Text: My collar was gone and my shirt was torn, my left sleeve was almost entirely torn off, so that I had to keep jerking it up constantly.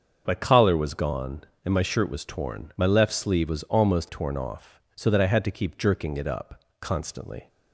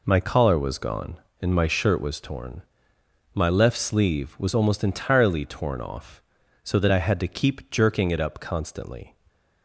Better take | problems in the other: second | starts louder than the rest; until 1.2 s; 7 dB // skips "entirely"; at 4.0 s // pauses between "up" and "constantly"; slight; at 6.6 s; 0.18 s long

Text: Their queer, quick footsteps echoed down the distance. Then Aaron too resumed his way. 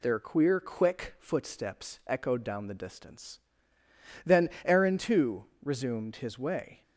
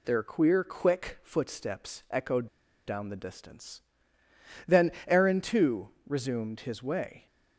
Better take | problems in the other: first | pauses between "echoed" and "down"; at 2.4 s; 0.41 s long // pauses between "Then" and "Aaron"; slight; at 4.9 s; 0.16 s long; slight in the first // pauses between "too" and "resumed"; slight; at 5.8 s; 0.18 s long; slight in the first

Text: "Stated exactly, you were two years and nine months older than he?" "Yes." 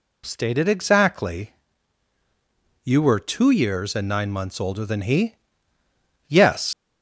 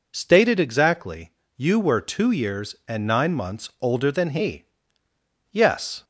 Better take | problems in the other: second | leaves "Yes" unfinished; at 6.7 s; 95 ms

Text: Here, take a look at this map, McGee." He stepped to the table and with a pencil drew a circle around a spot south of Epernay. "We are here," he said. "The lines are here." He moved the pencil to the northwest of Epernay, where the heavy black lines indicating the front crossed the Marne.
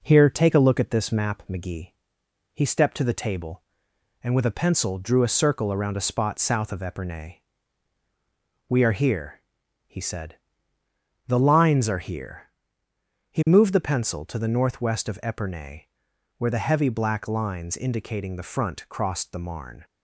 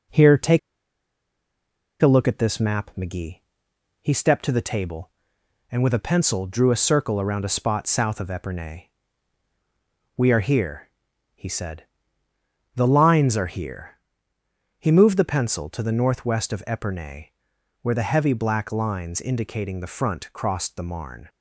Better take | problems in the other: first | pauses between "take" and "a"; strong; at 0.5 s; 1.4 s long

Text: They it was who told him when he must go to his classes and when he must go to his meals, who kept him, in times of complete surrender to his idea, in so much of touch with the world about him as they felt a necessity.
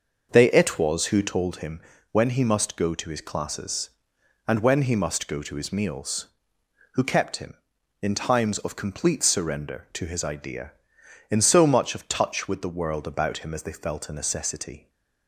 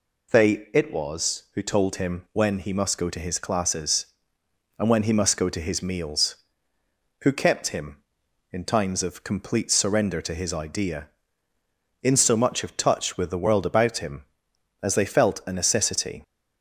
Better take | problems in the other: second | starts louder than the rest; noticeable; until 1.5 s; 6 dB // pauses between "him" and "when"; slight; at 1.8 s; 0.30 s long

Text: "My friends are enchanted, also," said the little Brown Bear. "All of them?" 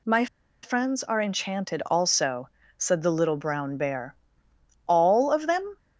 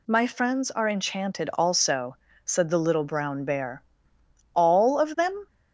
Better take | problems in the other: second | pauses between "My" and "friends"; at 0.2 s; 0.36 s long

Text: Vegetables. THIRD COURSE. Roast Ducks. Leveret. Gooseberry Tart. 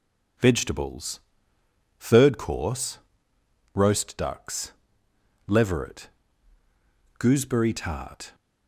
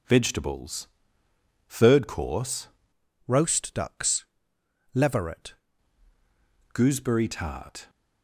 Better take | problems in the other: first | changes voice from "Roast" to "Leveret"; from 3.2 to 5.5 s; 2.3 s long

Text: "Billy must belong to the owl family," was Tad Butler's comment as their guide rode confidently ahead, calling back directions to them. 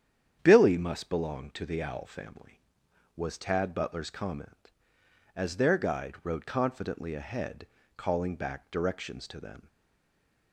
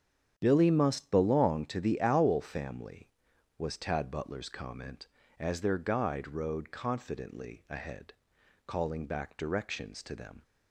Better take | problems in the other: second | starts louder than the rest; strong; until 1.4 s; 9 dB; strong in the second // stays silent after the last word; slight; from 9.6 s on; 0.9 s long

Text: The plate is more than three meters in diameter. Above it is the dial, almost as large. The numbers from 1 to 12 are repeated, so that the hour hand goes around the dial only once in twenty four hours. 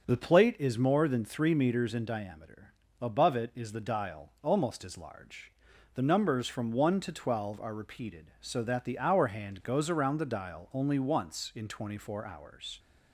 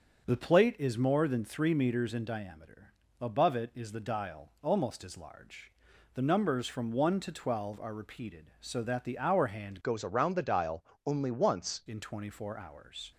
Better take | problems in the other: first | starts louder than the rest; until 1.3 s; 7 dB; also in the first // changes voice from "goes" to "once"; from 9.8 to 11.8 s; 2.0 s long // pauses between "dial" and "only"; slight; at 10.8 s; 0.22 s long

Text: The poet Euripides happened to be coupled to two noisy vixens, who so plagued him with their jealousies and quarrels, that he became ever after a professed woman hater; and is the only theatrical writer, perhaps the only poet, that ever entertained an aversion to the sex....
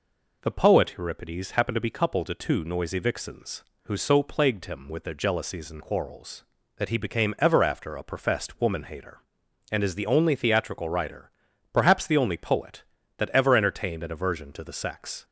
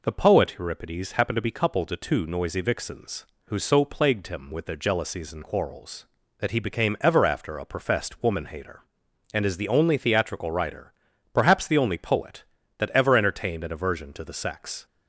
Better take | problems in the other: neither | none

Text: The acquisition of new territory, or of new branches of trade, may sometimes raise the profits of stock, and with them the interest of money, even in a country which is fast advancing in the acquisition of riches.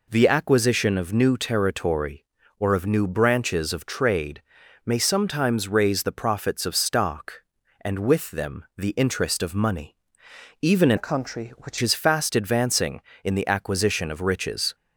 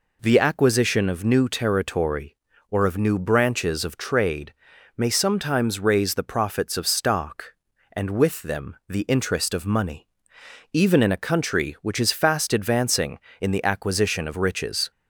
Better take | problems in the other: second | changes voice from "a" to "which"; from 10.9 to 11.7 s; 0.8 s long

